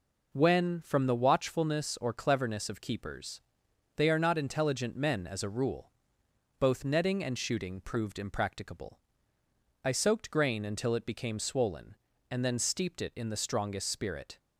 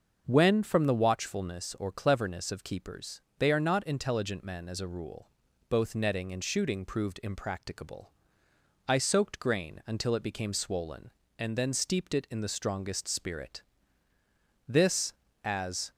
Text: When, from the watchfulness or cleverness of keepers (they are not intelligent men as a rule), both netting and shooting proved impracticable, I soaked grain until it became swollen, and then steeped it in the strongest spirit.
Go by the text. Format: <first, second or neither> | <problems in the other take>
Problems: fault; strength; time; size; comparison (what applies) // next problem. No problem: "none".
first | starts louder than the rest; until 1.2 s; 6 dB // goes on to say "This as"; noticeable; from 14.6 s on; 1.2 s long